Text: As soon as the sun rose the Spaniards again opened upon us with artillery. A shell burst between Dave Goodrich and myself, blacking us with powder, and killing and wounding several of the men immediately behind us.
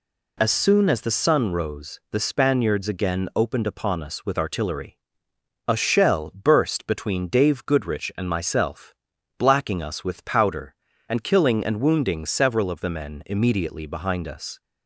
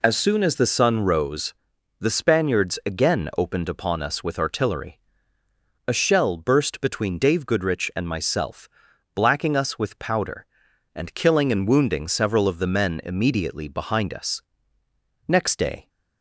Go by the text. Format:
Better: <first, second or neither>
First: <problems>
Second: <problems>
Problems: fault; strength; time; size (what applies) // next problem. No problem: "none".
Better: first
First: none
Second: pauses between "rose" and "the"; noticeable; at 1.5 s; 0.50 s long // goes on to say "Next day"; from 15.2 s on; 0.60 s long